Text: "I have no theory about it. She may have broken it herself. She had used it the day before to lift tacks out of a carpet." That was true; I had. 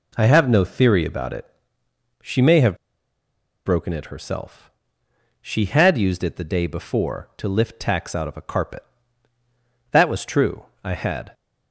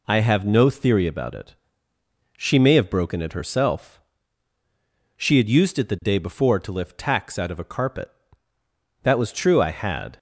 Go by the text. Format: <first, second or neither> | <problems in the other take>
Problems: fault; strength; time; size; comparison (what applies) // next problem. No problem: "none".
second | pauses between "have" and "broken"; noticeable; at 2.7 s; 0.90 s long